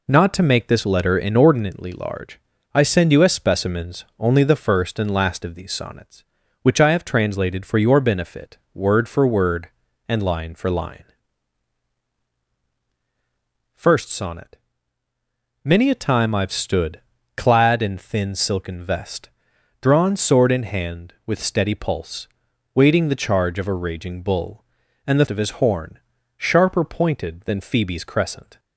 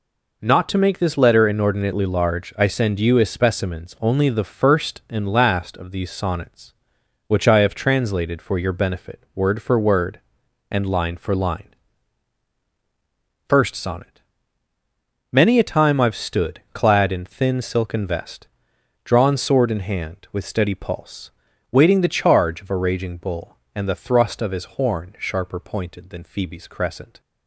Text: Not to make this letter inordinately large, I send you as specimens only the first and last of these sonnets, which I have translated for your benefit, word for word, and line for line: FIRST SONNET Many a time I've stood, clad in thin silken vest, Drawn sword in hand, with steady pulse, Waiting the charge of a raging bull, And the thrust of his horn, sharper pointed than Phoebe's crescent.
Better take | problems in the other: second | pauses between "SONNET" and "Many"; at 14.5 s; 1.1 s long; also in the second // skips "thrust"; at 25.2 s

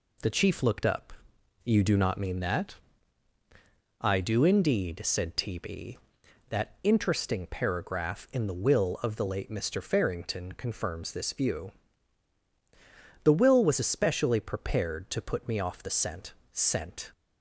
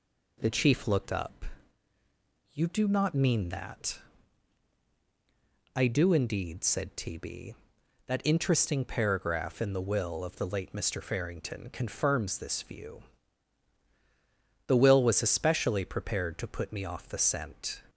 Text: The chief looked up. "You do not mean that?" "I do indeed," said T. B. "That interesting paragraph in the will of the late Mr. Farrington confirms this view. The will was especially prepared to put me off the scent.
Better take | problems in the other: second | says "scent" twice; at 16.5 s

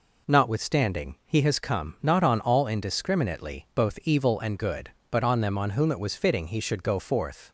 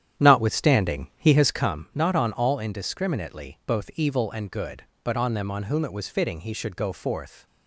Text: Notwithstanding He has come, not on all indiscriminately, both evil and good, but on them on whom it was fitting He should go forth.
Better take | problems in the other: first | starts louder than the rest; strong; until 1.9 s; 10 dB

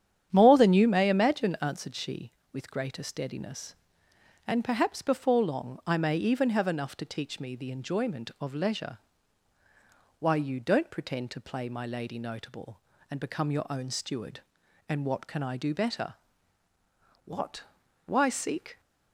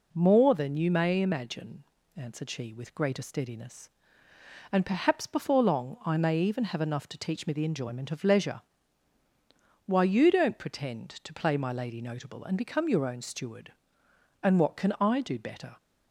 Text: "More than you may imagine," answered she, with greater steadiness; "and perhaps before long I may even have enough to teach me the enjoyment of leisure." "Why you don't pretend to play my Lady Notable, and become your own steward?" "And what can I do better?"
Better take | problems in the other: second | starts louder than the rest; strong; until 1.3 s; 9.5 dB // goes on to say "What Why seek"; from 17.2 s on; 1.5 s long

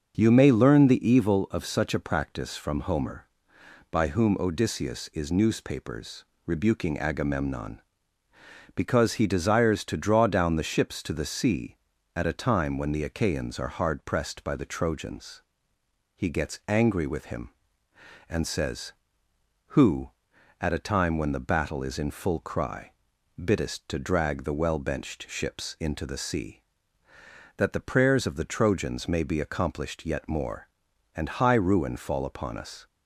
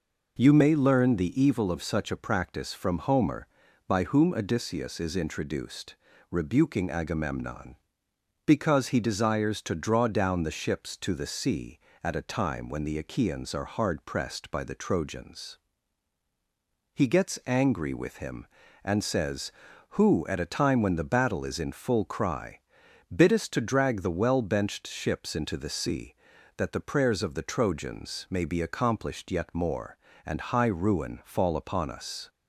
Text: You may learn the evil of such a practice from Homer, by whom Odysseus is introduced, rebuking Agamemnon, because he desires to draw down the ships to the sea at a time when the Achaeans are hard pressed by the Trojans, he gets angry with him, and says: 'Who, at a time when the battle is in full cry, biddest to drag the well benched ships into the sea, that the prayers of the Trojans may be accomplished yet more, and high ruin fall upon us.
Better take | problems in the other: second | starts louder than the rest; until 1.1 s; 6.5 dB // says "newspapers" for "introduced"; at 5.2 s

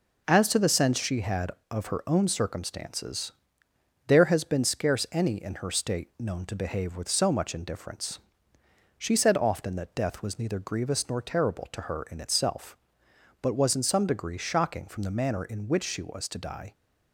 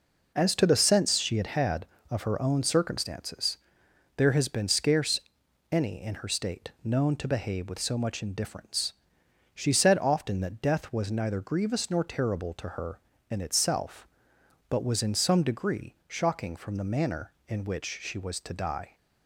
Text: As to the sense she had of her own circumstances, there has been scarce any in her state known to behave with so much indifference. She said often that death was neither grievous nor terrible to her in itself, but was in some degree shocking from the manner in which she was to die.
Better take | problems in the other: first | says "had" twice; at 1.4 s // pauses between "scarce" and "any"; noticeable; at 5.2 s; 0.50 s long

